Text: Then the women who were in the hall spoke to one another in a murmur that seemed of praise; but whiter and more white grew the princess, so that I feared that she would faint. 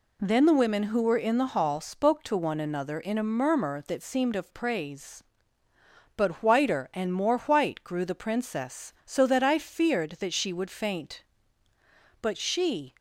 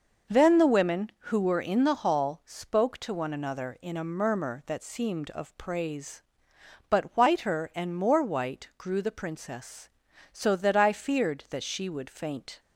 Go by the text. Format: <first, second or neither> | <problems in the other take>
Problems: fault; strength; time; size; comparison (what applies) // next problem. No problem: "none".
second | goes on to say "But she"; noticeable; from 12.2 s on; 0.72 s long